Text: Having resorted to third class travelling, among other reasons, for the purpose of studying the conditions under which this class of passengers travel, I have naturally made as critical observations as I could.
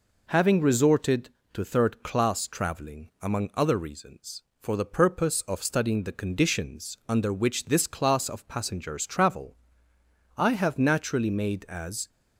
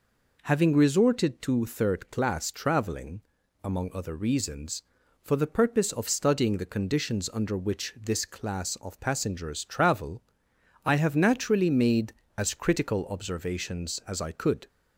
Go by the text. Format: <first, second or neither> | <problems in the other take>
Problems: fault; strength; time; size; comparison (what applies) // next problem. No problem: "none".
second | stops before "critical observations as I could"; at 12.0 s